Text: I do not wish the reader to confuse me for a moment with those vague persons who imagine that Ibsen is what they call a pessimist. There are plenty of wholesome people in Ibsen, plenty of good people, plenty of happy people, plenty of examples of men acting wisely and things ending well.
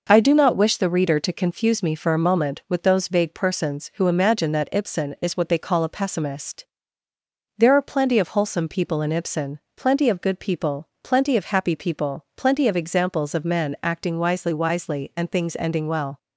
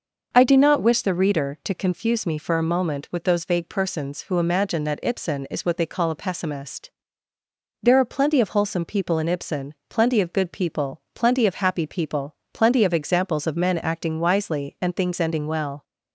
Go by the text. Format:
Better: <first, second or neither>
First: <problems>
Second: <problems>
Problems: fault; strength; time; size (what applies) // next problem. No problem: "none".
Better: second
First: says "wisely" twice; at 14.5 s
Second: none